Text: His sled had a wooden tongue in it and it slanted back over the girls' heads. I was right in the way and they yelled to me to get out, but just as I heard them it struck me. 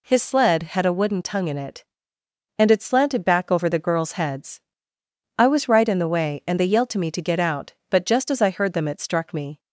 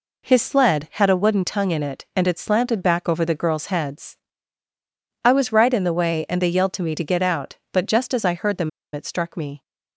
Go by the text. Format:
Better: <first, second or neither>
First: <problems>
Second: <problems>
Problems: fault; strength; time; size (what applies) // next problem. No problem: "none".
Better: first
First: none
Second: pauses between "them" and "it"; slight; at 8.6 s; 0.23 s long